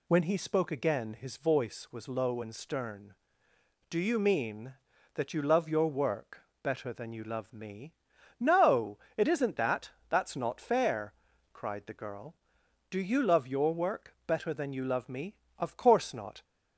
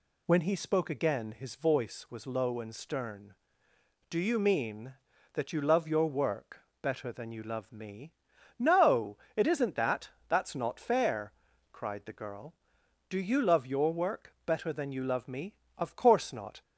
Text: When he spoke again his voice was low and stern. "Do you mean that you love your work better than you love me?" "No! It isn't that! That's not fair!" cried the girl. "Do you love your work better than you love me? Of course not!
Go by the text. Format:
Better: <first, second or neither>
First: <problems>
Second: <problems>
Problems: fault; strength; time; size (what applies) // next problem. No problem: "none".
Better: neither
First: pauses between "work" and "better"; slight; at 6.4 s; 0.18 s long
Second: pauses between "work" and "better"; slight; at 6.6 s; 0.18 s long